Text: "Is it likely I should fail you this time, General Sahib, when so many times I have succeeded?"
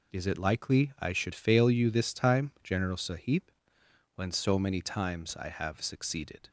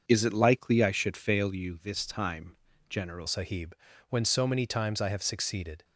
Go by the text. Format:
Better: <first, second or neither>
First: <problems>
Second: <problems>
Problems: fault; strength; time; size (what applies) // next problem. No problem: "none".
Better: first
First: none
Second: starts louder than the rest; until 1.0 s; 6.5 dB // changes voice at "Sahib"; from 3.2 s on; 2.6 s long